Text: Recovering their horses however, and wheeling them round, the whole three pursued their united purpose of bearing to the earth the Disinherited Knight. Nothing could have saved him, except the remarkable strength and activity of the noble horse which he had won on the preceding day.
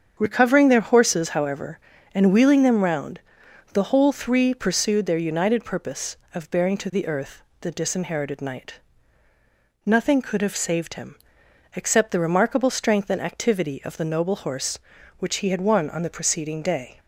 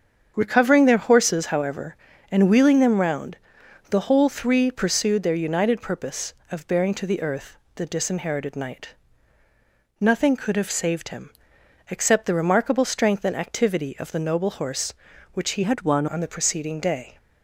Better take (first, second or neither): first